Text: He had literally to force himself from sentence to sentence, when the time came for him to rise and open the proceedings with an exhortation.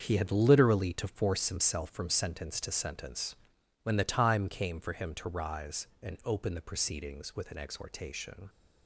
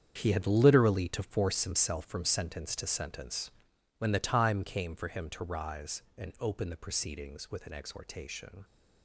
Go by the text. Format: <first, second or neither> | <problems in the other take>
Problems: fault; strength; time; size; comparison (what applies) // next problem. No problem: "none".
first | gets quieter; strong; throughout; 12.5 dB // starts louder than the rest; strong; until 1.1 s; 8 dB; also in the first